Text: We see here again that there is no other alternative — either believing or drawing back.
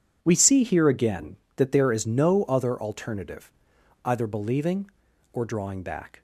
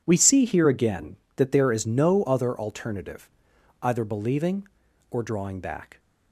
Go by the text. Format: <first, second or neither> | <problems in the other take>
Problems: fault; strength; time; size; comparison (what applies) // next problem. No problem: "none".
neither | none